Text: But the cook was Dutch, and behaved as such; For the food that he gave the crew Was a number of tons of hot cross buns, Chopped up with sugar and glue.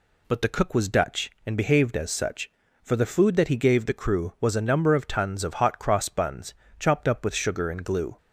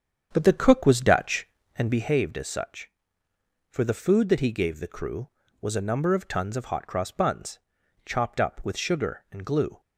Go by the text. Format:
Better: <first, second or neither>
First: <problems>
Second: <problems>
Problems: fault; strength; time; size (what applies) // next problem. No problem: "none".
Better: first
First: none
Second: starts louder than the rest; strong; until 2.0 s; 8 dB